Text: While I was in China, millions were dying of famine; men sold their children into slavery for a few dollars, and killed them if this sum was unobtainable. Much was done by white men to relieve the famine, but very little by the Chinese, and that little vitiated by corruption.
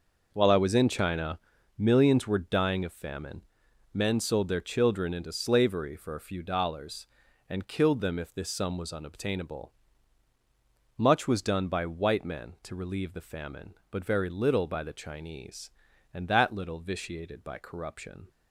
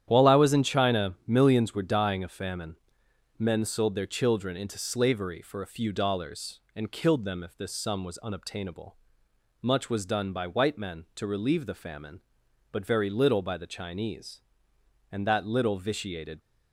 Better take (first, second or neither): first